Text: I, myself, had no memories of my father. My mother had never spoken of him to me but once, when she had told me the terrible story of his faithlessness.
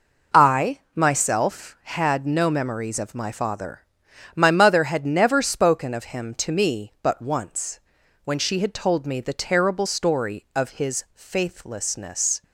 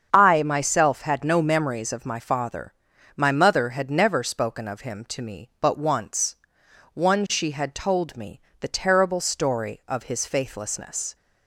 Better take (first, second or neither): first